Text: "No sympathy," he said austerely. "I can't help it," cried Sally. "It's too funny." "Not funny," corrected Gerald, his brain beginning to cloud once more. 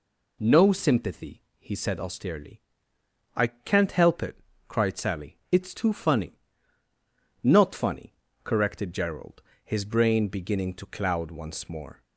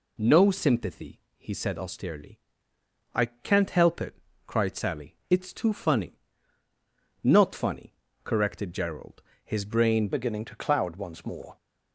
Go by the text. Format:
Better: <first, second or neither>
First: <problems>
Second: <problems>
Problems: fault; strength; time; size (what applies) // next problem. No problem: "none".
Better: first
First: none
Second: changes voice at "beginning"; from 10.1 s on; 1.4 s long